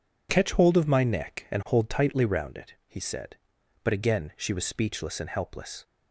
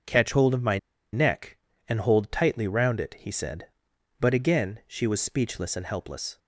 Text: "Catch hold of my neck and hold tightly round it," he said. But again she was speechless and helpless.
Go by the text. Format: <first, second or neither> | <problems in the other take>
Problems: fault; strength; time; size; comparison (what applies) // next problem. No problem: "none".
first | starts louder than the rest; until 1.4 s; 6 dB // pauses between "my" and "neck"; slight; at 0.7 s; 0.33 s long